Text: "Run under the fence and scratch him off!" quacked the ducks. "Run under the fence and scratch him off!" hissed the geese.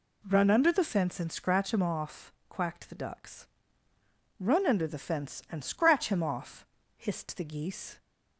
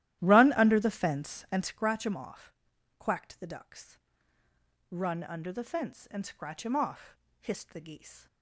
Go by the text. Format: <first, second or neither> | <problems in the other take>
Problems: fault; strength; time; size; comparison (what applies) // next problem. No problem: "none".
first | starts louder than the rest; strong; until 1.8 s; 13.5 dB